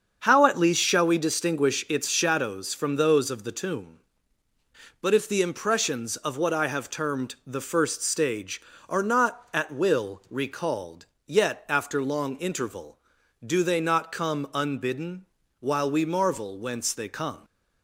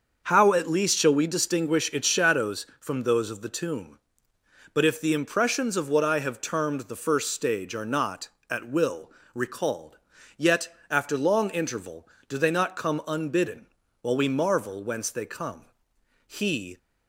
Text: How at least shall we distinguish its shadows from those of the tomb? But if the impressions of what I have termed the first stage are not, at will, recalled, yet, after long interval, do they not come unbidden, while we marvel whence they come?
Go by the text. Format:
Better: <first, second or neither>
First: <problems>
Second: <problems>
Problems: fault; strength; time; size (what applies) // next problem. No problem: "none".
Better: first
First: starts louder than the rest; until 1.2 s; 7 dB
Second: starts louder than the rest; until 1.2 s; 6.5 dB // goes on to say "He"; from 16.2 s on; 0.52 s long